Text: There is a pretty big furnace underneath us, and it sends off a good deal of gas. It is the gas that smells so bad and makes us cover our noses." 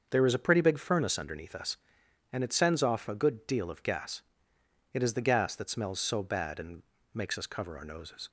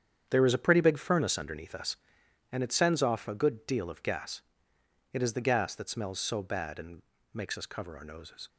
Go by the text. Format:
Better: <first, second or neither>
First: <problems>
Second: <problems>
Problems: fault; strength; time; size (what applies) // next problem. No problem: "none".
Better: first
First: starts louder than the rest; until 1.1 s; 6.5 dB // pauses between "and" and "makes"; slight; at 6.8 s; 0.30 s long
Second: gets quieter; strong; throughout; 11 dB // starts louder than the rest; strong; until 1.3 s; 8.5 dB // pauses between "and" and "makes"; slight; at 7.0 s; 0.30 s long